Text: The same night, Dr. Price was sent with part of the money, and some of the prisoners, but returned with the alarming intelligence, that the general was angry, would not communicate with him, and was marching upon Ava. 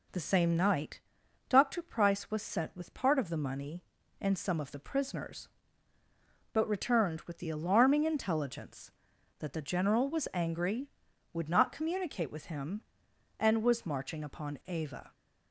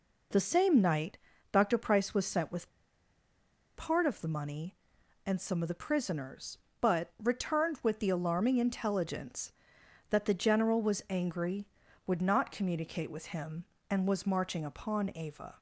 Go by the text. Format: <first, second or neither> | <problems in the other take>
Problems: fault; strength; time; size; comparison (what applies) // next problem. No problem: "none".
first | pauses between "with" and "part"; at 2.6 s; 1.0 s long